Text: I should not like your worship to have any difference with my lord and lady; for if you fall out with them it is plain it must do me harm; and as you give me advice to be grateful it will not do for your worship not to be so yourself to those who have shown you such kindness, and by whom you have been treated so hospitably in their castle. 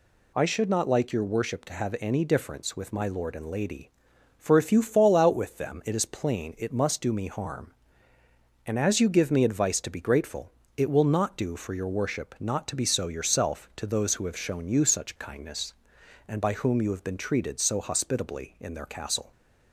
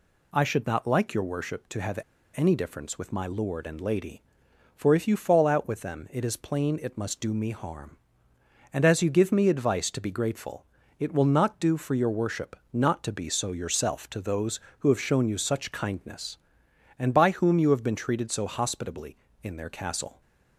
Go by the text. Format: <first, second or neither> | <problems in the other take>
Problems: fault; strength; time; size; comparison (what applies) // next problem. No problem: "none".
first | pauses between "have" and "any"; slight; at 1.9 s; 0.36 s long // pauses between "grateful" and "it"; slight; at 10.6 s; 0.34 s long; slight in the first // pauses between "worship" and "not"; slight; at 12.5 s; 0.16 s long